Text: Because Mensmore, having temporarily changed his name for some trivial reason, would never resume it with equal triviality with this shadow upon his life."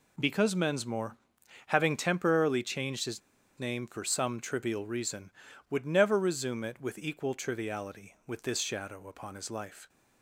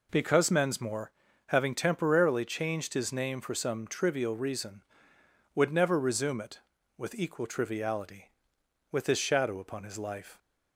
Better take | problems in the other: second | pauses between "his" and "name"; at 3.2 s; 0.38 s long

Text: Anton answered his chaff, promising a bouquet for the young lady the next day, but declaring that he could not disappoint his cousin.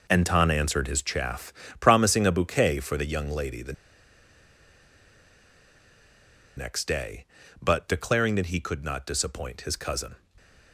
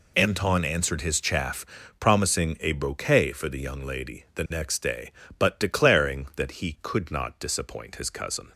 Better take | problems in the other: second | pauses between "the" and "next"; strong; at 3.7 s; 2.8 s long

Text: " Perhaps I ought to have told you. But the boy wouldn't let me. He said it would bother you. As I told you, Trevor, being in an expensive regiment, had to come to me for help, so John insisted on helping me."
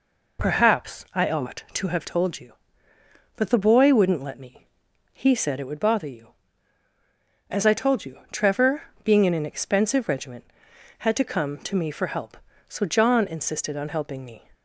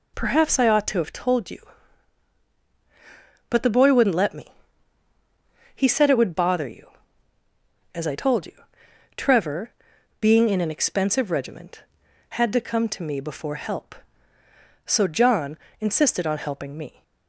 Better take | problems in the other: first | says "before" for "for"; at 13.2 s // pauses between "John" and "insisted"; slight; at 15.5 s; 0.24 s long

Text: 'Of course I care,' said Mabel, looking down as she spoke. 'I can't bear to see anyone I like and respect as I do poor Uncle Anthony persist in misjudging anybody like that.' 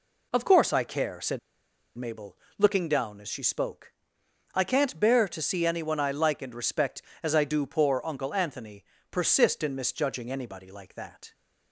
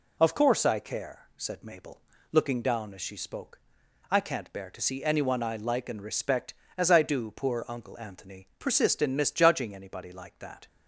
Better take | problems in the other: second | pauses between "said" and "Mabel"; noticeable; at 1.3 s; 0.57 s long // pauses between "Anthony" and "persist"; slight; at 8.8 s; 0.24 s long

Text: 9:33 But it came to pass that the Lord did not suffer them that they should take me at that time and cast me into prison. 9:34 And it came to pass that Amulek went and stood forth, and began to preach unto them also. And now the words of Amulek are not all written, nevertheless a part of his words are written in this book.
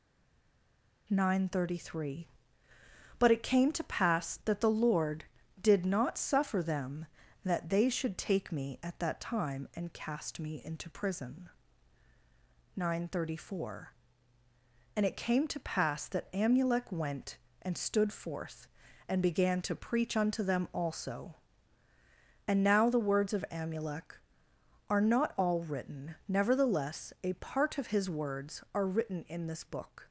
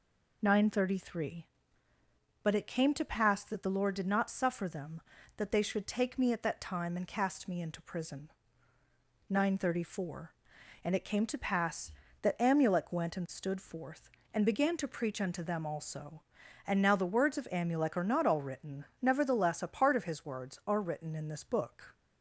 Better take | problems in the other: second | stays silent before the first word; until 1.0 s; 1.0 s long

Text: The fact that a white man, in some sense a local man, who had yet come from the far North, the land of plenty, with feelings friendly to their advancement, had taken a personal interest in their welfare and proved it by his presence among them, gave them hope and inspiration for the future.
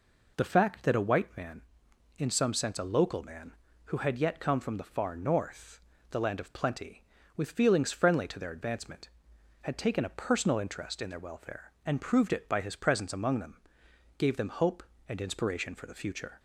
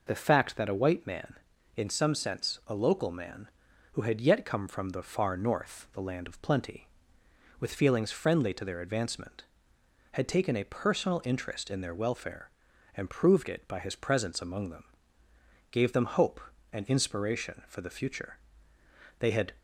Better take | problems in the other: first | goes on to say "They had"; slight; from 19.1 s on; 0.34 s long

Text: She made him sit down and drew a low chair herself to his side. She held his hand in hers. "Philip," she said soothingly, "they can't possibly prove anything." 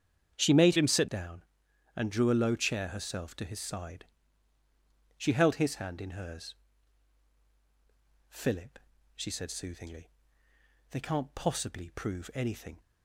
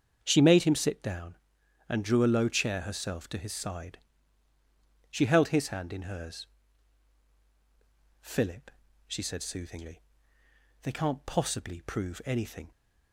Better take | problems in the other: second | starts louder than the rest; strong; until 1.3 s; 8 dB; strong in the second // changes voice from "him" to "sit"; from 0.7 to 1.0 s; 0.3 s long

